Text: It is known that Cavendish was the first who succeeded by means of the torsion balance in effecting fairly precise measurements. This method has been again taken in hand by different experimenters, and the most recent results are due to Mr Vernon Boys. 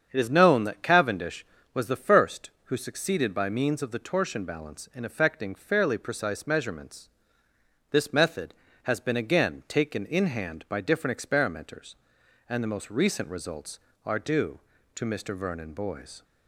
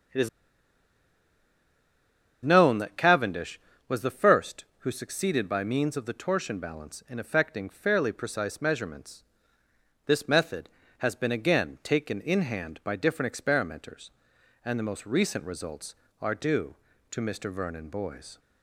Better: first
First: starts louder than the rest; strong; until 1.1 s; 7.5 dB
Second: starts louder than the rest; strong; until 3.2 s; 7.5 dB // pauses between "is" and "known"; strong; at 0.2 s; 2.1 s long

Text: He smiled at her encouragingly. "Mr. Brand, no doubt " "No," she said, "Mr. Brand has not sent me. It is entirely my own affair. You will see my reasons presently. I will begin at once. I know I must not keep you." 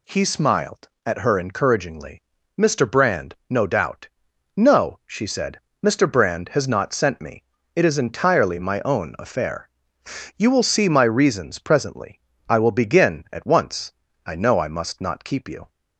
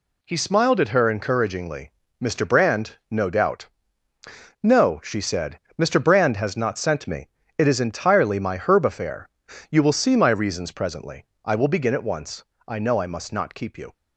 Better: first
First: none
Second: says "herb" for "own"; at 8.5 s

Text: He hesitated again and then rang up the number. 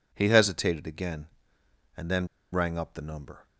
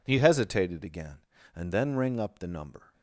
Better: second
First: pauses between "then" and "rang"; slight; at 2.2 s; 0.25 s long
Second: none

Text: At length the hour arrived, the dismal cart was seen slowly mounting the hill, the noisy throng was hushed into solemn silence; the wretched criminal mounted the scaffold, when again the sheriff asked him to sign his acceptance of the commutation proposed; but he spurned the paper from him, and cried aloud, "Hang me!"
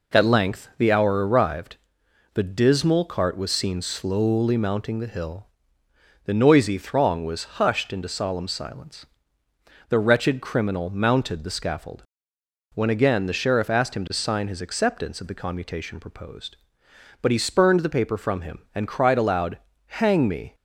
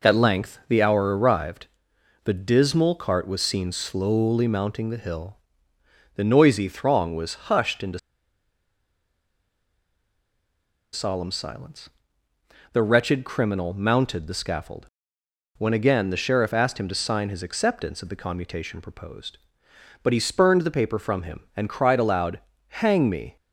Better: first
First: none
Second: pauses between "into" and "solemn"; strong; at 7.9 s; 2.9 s long

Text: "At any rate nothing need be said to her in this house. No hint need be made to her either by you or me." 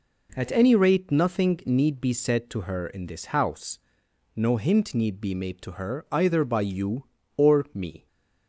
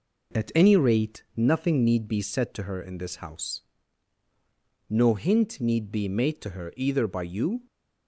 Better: first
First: none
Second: stops before "or me"; at 7.6 s

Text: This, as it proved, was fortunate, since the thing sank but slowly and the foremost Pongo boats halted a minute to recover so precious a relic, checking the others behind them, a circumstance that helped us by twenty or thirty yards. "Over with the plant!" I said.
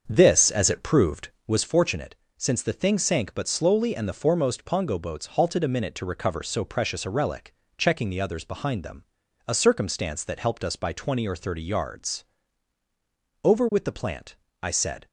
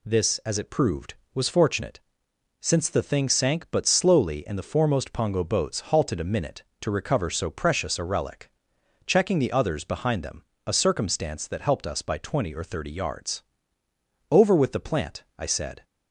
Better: second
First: starts louder than the rest; until 1.6 s; 7 dB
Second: none

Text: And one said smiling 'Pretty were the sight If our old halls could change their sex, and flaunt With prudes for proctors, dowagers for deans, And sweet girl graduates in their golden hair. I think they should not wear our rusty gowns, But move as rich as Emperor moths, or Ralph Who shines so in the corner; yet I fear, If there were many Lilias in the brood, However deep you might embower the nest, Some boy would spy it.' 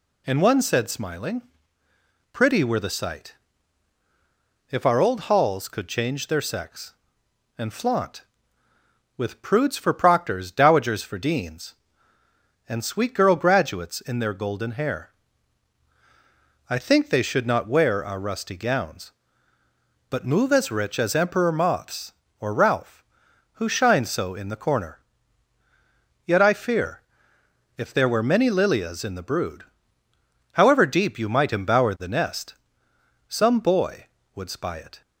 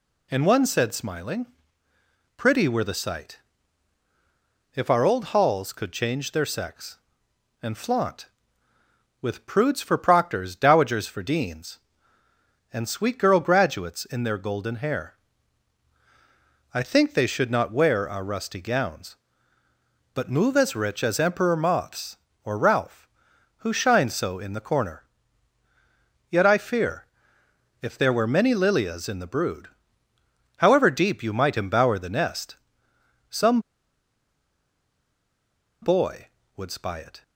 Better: first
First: pauses between "smiling" and "Pretty"; noticeable; at 1.4 s; 0.90 s long // pauses between "sight" and "If"; strong; at 3.3 s; 1.3 s long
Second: pauses between "smiling" and "Pretty"; noticeable; at 1.4 s; 0.90 s long // pauses between "sight" and "If"; strong; at 3.3 s; 1.3 s long // pauses between "Some" and "boy"; strong; at 33.6 s; 2.2 s long

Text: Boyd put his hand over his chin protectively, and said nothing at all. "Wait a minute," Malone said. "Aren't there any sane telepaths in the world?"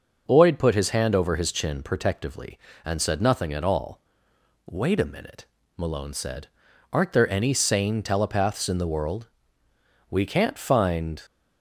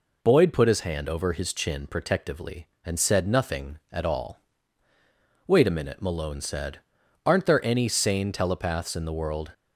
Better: second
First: goes on to say "We can't find"; noticeable; from 10.1 s on; 1.1 s long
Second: none

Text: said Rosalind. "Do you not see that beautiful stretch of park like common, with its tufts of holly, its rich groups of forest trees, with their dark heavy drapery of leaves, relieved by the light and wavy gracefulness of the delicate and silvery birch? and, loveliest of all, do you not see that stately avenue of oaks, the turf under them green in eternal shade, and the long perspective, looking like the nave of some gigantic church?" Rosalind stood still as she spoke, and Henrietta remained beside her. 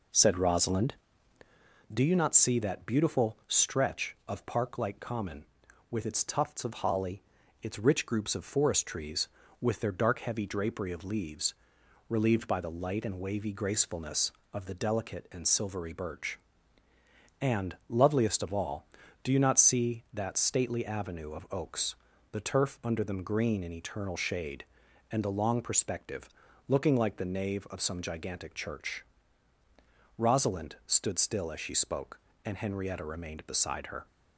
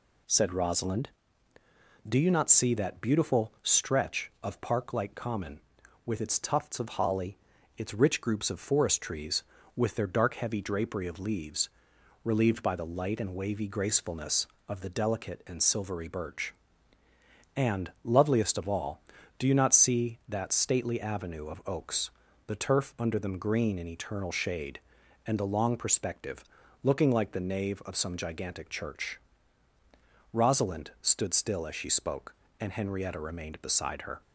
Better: second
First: starts louder than the rest; noticeable; until 1.7 s; 4 dB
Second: none

